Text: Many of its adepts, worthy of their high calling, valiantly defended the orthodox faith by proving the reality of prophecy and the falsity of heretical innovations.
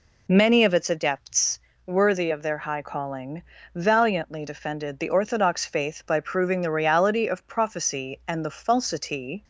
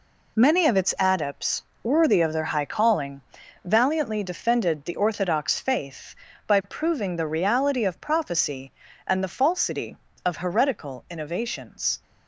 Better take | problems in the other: second | stops before "of heretical innovations"; at 9.4 s

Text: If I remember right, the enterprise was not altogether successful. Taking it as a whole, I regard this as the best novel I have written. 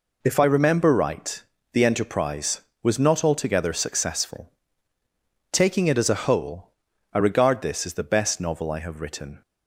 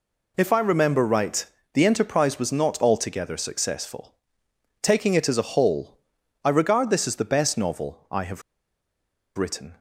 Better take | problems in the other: first | pauses between "have" and "written"; noticeable; at 8.4 s; 0.94 s long

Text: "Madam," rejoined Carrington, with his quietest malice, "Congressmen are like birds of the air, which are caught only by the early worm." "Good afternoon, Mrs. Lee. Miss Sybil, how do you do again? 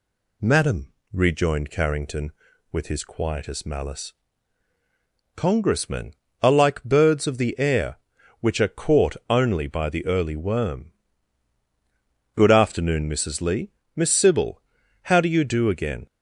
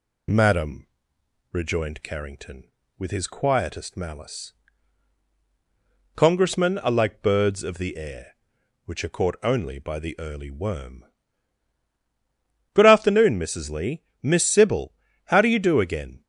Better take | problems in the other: neither | none

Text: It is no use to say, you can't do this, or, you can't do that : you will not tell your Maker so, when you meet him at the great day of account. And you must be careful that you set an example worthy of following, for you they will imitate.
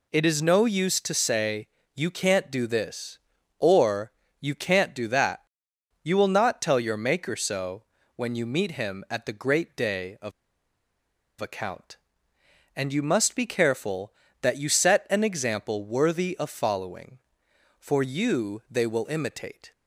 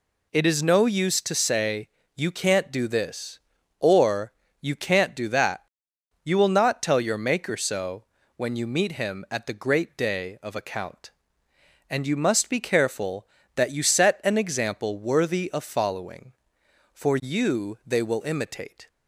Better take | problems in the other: second | pauses between "of" and "account"; at 10.3 s; 1.0 s long

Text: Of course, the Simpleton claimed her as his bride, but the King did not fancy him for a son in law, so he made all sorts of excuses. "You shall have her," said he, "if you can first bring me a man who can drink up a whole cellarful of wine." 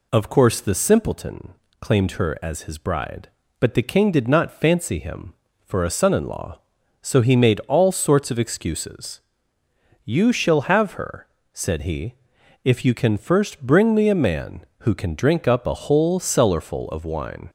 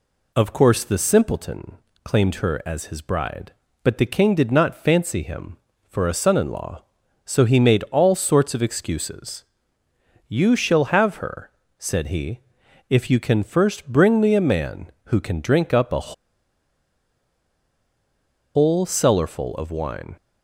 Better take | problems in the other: first | pauses between "Simpleton" and "claimed"; slight; at 1.7 s; 0.28 s long; slight in the first // pauses between "a" and "whole"; strong; at 16.1 s; 2.4 s long

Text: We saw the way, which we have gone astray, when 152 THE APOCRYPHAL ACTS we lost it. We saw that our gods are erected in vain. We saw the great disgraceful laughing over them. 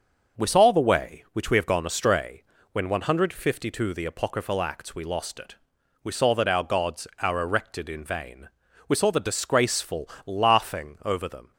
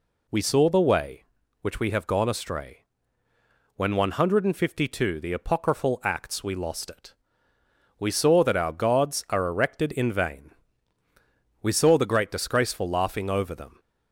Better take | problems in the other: second | skips "great"; at 9.2 s // pauses between "disgraceful" and "laughing"; slight; at 10.1 s; 0.16 s long

